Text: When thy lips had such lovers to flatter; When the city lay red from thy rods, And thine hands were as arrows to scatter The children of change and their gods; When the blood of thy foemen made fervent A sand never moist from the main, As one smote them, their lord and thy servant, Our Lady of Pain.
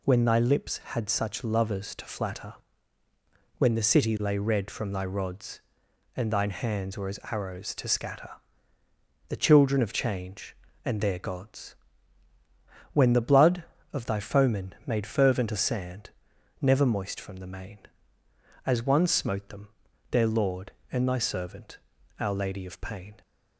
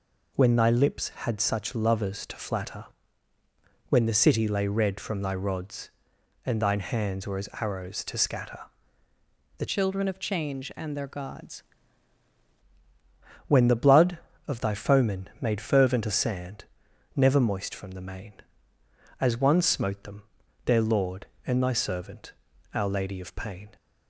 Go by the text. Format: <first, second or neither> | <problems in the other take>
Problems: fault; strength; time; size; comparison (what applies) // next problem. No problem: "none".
first | pauses between "scatter" and "The"; noticeable; at 8.6 s; 0.98 s long; noticeable in the first // changes voice from "children" to "gods"; from 9.6 to 11.6 s; 2.0 s long // pauses between "sand" and "never"; noticeable; at 16.6 s; 0.52 s long; noticeable in the first